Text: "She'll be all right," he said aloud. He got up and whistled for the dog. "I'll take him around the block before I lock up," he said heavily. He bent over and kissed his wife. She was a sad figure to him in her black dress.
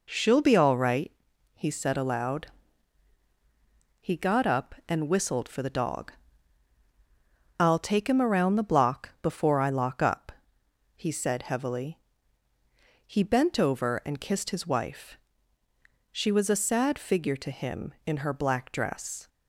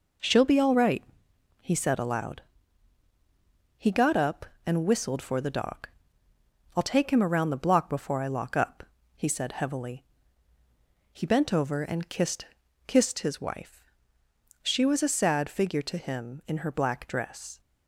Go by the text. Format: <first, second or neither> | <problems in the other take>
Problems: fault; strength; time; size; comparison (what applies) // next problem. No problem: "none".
first | says "kissed" twice; at 12.8 s